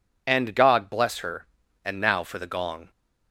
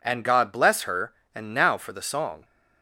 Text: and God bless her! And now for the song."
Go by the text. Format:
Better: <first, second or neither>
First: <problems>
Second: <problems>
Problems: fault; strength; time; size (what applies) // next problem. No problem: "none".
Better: second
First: says "gong" for "song"; at 2.4 s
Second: none